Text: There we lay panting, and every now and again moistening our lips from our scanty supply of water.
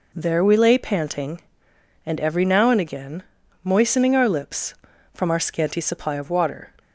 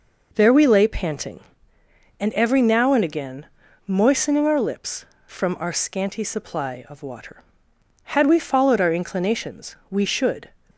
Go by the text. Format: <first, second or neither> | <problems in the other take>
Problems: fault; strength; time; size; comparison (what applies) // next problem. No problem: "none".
first | pauses between "again" and "moistening"; at 3.4 s; 0.42 s long; also in the first // goes on to say "Had we followed our inclinations we should"; strong; from 8.0 s on; 2.4 s long